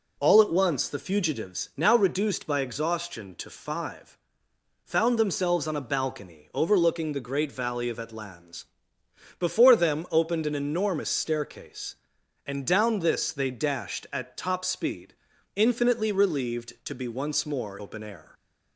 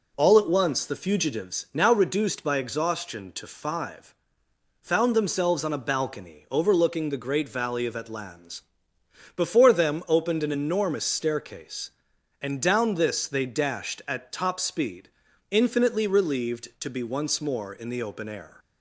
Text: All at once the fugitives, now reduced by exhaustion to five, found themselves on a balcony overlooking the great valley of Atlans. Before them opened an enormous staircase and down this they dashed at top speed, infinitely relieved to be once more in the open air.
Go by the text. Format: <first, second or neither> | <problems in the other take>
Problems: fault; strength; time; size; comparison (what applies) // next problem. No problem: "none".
second | skips "in the"; at 17.7 s